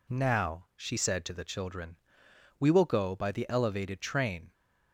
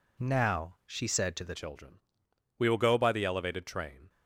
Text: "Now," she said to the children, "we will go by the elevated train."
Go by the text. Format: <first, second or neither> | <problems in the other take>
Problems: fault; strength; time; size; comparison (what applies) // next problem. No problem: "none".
first | changes voice at "children"; from 1.5 s on; 2.5 s long